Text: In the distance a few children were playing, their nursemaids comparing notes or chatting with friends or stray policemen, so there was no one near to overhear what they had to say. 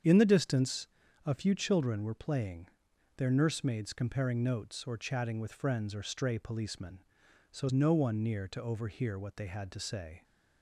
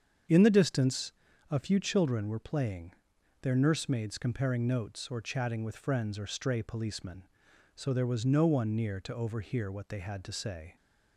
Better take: second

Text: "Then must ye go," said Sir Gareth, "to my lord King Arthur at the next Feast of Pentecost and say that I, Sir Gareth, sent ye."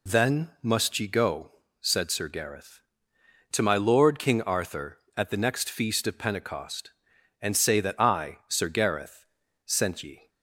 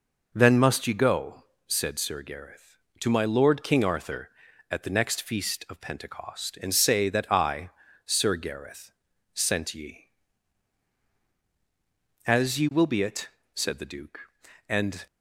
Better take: first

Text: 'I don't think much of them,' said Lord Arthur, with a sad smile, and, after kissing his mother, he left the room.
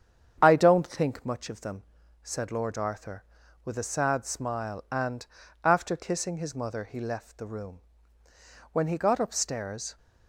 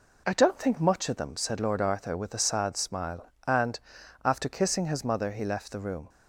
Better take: second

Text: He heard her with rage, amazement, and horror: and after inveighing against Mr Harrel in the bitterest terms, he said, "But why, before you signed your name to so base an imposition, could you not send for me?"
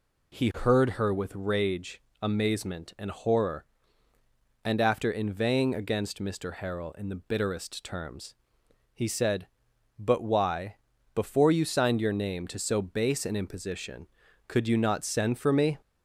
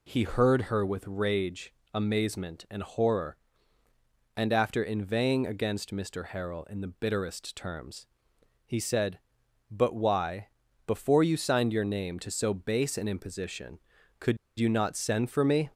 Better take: first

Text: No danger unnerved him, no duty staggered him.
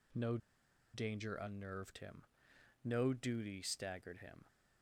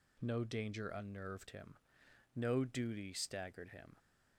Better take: second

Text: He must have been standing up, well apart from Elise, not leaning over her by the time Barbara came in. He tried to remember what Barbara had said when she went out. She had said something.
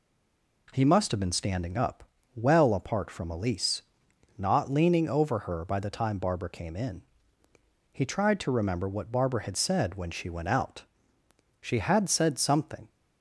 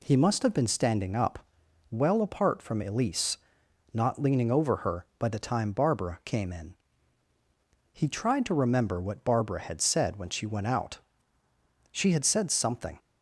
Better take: second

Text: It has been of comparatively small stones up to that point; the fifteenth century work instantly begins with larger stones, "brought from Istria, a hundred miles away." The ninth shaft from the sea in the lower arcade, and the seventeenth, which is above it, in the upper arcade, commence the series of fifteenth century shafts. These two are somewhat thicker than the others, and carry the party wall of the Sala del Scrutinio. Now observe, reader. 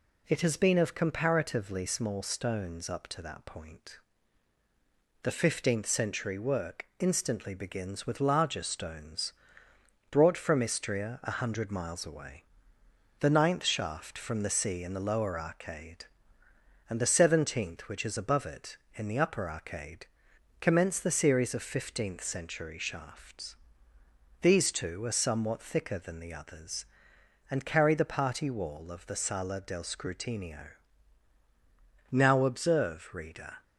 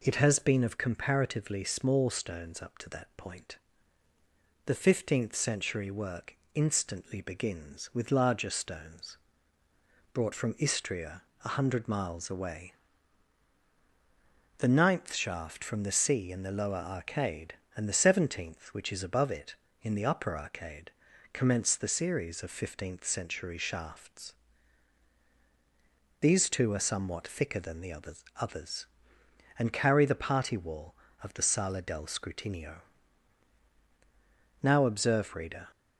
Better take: first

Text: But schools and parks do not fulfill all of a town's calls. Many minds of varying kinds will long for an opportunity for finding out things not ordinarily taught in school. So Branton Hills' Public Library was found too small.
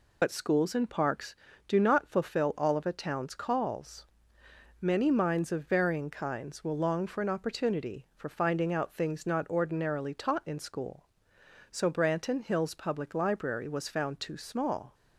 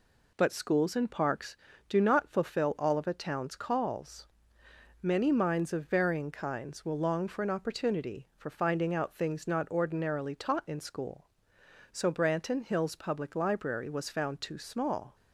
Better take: second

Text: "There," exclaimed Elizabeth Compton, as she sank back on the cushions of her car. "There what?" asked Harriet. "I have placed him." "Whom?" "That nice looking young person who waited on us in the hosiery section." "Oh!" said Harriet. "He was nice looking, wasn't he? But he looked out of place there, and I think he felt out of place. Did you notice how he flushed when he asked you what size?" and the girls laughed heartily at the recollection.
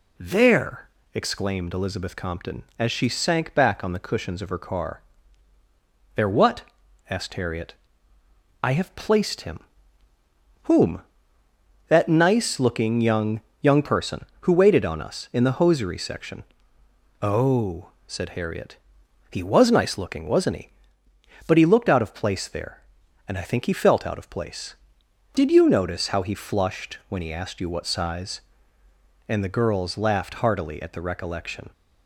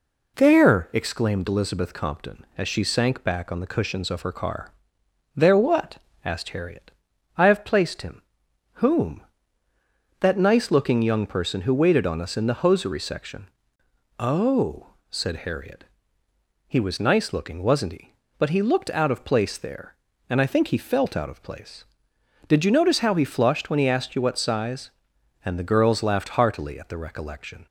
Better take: second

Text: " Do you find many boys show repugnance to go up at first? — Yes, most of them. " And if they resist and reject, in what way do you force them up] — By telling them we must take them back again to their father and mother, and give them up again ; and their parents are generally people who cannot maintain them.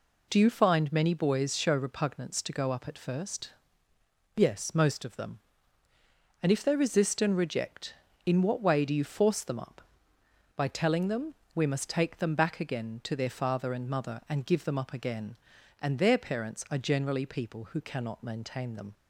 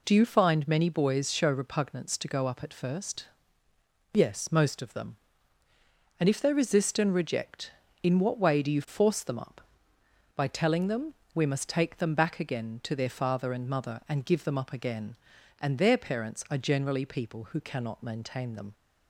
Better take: neither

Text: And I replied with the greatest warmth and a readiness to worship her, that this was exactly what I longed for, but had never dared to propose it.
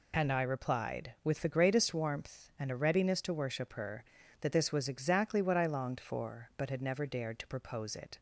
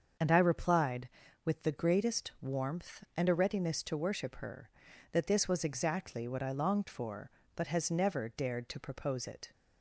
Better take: first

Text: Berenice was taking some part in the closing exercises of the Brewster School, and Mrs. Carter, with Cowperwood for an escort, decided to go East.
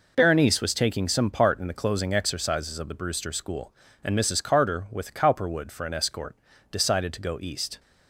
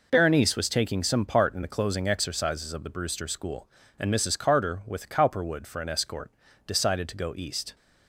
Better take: neither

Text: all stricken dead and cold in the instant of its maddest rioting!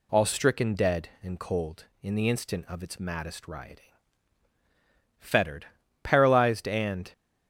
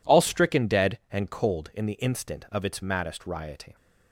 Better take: second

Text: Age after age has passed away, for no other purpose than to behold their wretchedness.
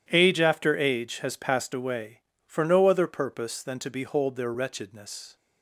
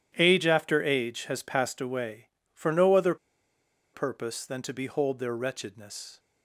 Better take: first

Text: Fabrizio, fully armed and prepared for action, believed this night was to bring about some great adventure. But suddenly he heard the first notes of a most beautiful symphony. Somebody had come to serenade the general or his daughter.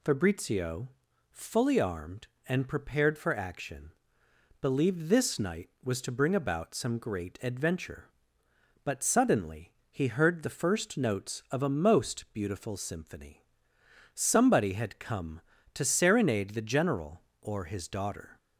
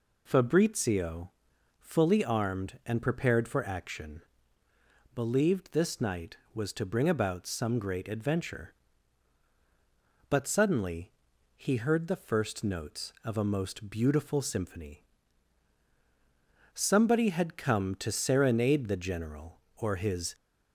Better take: first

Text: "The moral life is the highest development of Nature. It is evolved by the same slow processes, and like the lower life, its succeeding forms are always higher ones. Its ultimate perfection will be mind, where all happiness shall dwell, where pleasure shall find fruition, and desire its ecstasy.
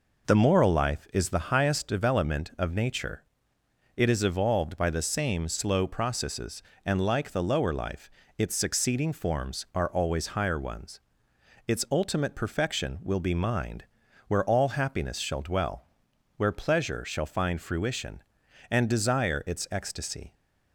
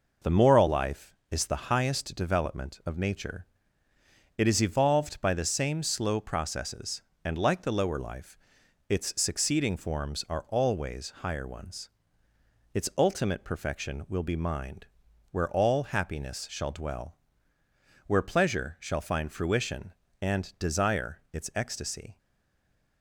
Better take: first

